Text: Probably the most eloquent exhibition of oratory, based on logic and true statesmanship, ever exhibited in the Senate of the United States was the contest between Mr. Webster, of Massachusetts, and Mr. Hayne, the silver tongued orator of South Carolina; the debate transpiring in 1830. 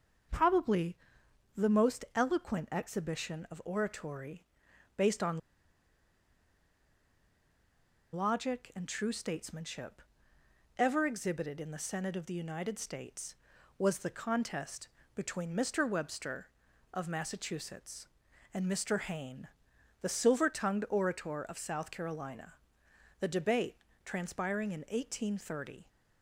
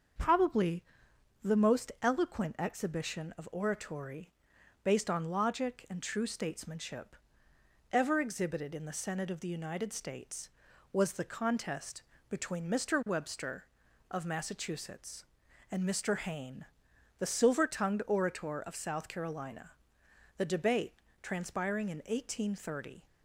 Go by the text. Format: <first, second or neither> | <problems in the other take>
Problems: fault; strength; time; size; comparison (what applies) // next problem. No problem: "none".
second | starts louder than the rest; until 1.9 s; 6.5 dB; also in the second // pauses between "Probably" and "the"; noticeable; at 0.9 s; 0.60 s long; noticeable in the second // pauses between "on" and "logic"; strong; at 5.3 s; 2.7 s long // pauses between "contest" and "between"; slight; at 14.8 s; 0.28 s long; slight in the second // pauses between "debate" and "transpiring"; slight; at 23.7 s; 0.26 s long; slight in the second